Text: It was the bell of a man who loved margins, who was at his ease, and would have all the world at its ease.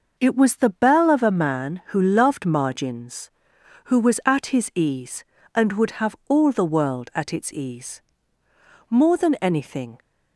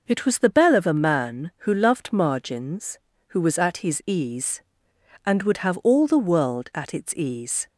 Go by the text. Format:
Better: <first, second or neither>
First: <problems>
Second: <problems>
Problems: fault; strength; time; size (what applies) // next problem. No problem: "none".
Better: second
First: goes on to say "More than anything"; noticeable; from 8.8 s on; 1.1 s long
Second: none